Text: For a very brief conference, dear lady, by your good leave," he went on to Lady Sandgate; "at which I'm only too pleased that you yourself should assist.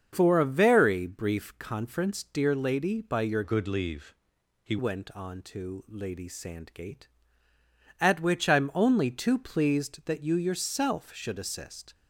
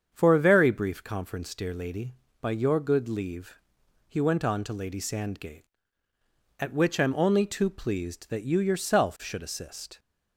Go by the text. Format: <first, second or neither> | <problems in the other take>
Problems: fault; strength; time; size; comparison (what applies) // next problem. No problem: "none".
second | starts louder than the rest; until 1.1 s; 7 dB; strong in the second // changes voice from "good" to "he"; from 3.4 to 4.7 s; 1.3 s long